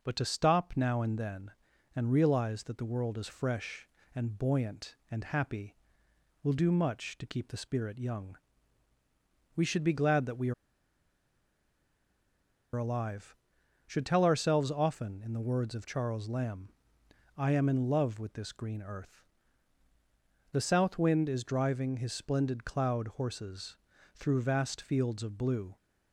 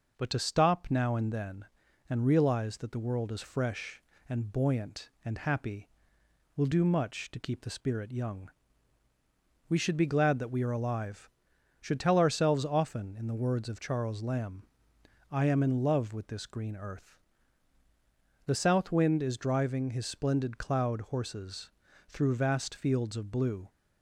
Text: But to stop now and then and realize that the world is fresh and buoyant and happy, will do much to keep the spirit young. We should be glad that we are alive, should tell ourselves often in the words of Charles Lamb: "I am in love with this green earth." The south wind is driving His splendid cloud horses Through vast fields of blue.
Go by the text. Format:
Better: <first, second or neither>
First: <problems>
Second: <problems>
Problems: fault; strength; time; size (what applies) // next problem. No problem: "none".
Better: second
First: pauses between "are" and "alive"; strong; at 10.5 s; 2.2 s long // pauses between "horses" and "Through"; slight; at 23.7 s; 0.36 s long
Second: pauses between "horses" and "Through"; slight; at 21.7 s; 0.36 s long